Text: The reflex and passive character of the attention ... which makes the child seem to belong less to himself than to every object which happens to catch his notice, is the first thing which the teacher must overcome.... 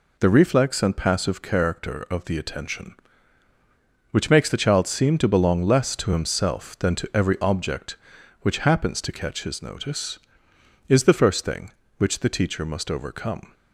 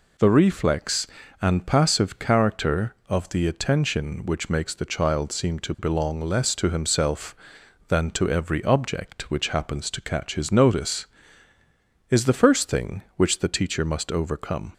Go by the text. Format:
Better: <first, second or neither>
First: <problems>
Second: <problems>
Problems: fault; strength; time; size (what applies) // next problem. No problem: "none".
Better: neither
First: none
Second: none